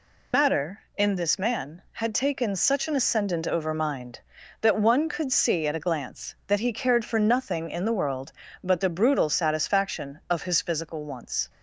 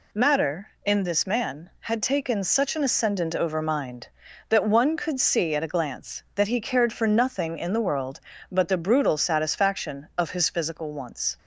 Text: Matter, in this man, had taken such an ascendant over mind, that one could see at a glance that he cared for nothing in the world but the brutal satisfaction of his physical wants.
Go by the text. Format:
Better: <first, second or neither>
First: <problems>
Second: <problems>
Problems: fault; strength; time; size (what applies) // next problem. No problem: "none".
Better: second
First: loses the start of "Matter"; at 0.3 s; 80 ms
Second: none